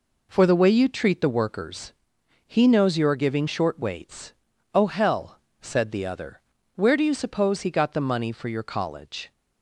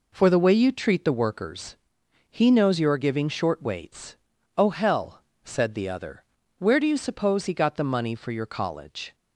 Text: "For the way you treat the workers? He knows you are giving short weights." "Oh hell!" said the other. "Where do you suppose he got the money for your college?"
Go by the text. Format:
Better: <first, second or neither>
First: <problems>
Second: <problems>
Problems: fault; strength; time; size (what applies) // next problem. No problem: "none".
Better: neither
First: none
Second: none